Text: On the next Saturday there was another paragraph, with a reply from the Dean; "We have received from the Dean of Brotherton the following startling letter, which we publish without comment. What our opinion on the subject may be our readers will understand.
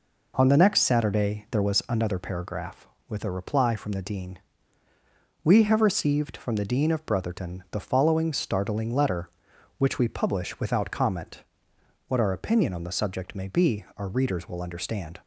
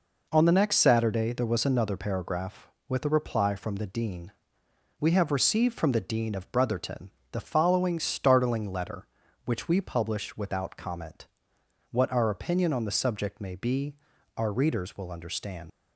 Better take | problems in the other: first | pauses between "Brotherton" and "the"; slight; at 7.1 s; 0.20 s long // pauses between "be" and "our"; at 13.9 s; 0.40 s long // leaves "understand" unfinished; at 15.7 s; 70 ms

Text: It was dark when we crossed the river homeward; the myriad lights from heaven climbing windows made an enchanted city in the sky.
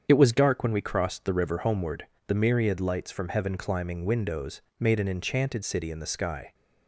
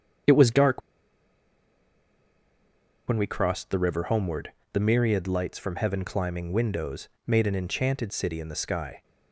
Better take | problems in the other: first | starts louder than the rest; strong; until 3.5 s; 7.5 dB; strong in the first // pauses between "dark" and "when"; strong; at 0.8 s; 2.2 s long // pauses between "windows" and "made"; slight; at 7.0 s; 0.20 s long; slight in the first

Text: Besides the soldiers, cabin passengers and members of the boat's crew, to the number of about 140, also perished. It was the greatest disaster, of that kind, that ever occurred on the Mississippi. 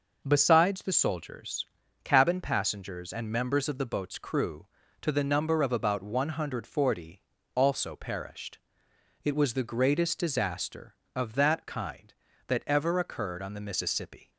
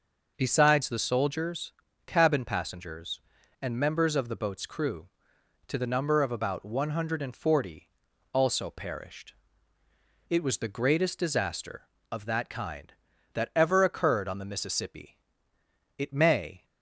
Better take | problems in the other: first | goes on to say "It may"; noticeable; from 15.9 s on; 0.68 s long

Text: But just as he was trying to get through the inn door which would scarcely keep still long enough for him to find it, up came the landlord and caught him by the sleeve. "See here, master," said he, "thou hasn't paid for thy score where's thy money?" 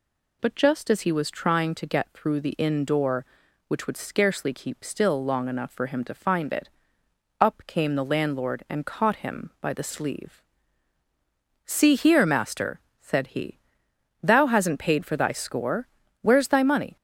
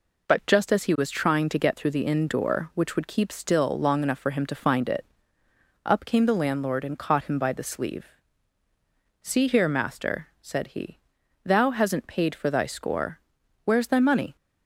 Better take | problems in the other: first | skips "scarcely"; at 3.0 s // pauses between "score" and "where's"; at 13.1 s; 0.44 s long; slight in the first

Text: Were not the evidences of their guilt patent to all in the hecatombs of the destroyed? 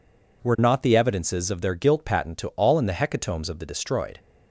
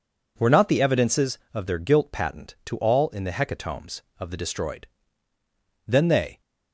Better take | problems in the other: first | goes on to say "Then they"; from 5.8 s on; 0.54 s long

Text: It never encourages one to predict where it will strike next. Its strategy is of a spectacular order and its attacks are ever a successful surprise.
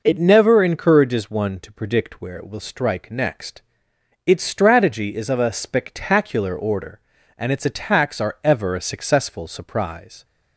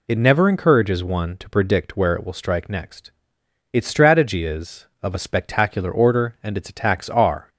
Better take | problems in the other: first | stops before "ever a successful surprise"; at 7.4 s

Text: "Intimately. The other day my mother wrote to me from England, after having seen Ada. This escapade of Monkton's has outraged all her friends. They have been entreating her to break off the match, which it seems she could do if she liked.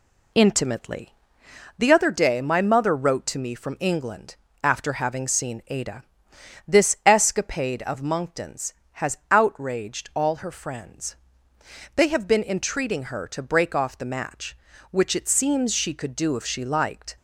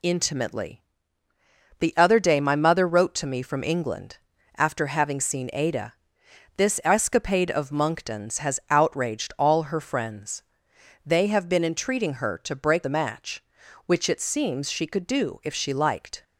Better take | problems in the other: first | skips "off"; at 12.8 s

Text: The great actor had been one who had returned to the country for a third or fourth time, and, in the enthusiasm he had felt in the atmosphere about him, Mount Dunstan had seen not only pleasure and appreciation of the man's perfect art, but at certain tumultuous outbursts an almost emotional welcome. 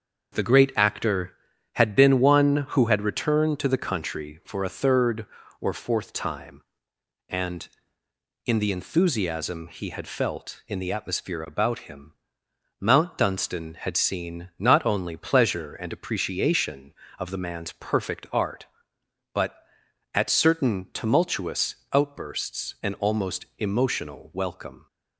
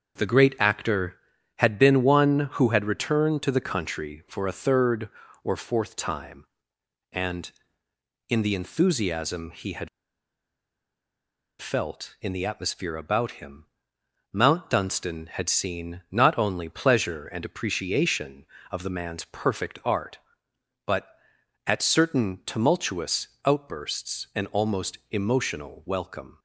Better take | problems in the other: first | starts louder than the rest; until 1.6 s; 6.5 dB; also in the first // pauses between "had" and "felt"; strong; at 9.8 s; 1.7 s long // pauses between "tumultuous" and "outbursts"; slight; at 23.2 s; 0.16 s long; slight in the first // pauses between "almost" and "emotional"; slight; at 24.9 s; 0.16 s long; slight in the first

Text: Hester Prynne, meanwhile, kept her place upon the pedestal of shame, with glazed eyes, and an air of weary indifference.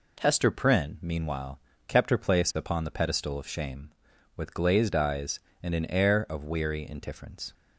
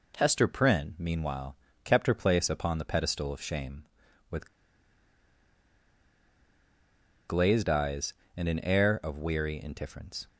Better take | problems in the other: first | pauses between "with" and "glazed"; strong; at 4.4 s; 2.8 s long

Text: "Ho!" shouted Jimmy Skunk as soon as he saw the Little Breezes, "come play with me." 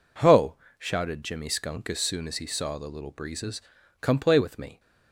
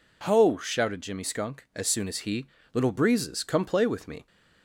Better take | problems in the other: first | skips "saw the"; at 2.5 s

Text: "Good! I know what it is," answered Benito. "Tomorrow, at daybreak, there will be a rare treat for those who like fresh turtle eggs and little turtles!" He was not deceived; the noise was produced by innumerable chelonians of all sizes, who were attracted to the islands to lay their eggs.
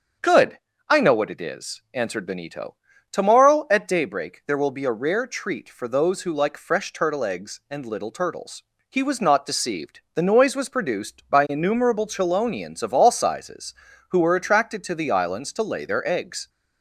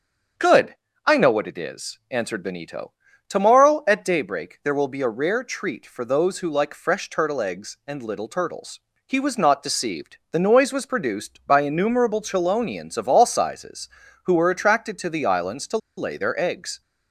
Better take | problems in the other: first | starts louder than the rest; until 1.6 s; 7 dB; also in the first // pauses between "to" and "lay"; slight; at 15.7 s; 0.19 s long

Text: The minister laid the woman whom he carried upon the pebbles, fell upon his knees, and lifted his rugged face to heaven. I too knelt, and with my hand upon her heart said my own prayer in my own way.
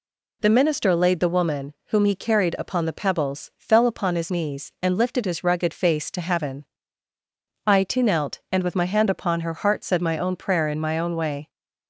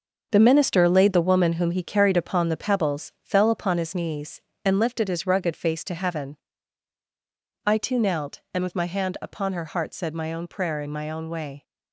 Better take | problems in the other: first | gets quieter; strong; throughout; 8.5 dB

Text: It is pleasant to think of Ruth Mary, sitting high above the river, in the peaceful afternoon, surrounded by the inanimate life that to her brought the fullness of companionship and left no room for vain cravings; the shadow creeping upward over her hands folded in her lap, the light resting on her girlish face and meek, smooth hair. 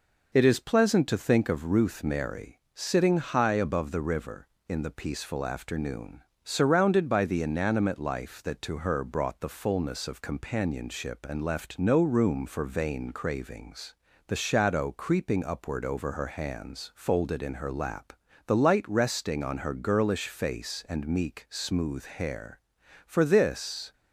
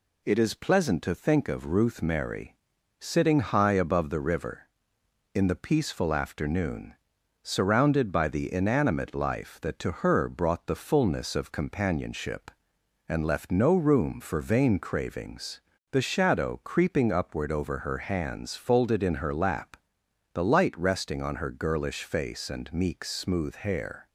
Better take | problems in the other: second | goes on to say "For this"; noticeable; from 23.0 s on; 0.86 s long

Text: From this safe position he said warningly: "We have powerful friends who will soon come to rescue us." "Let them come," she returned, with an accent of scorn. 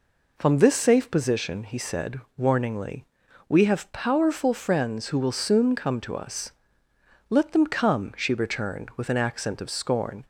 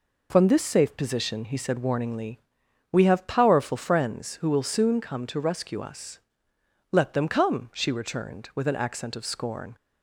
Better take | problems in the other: second | pauses between "said" and "warningly"; slight; at 2.2 s; 0.16 s long // skips "rescue"; at 6.1 s

